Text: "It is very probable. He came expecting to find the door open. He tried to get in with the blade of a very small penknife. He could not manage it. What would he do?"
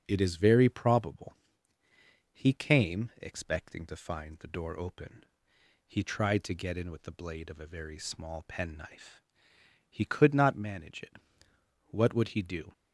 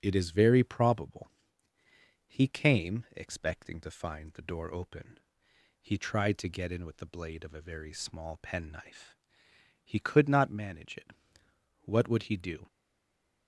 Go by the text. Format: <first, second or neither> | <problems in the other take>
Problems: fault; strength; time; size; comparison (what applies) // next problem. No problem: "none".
first | starts louder than the rest; until 1.0 s; 6 dB; also in the first // stays silent after the last word; slight; from 12.6 s on; 0.8 s long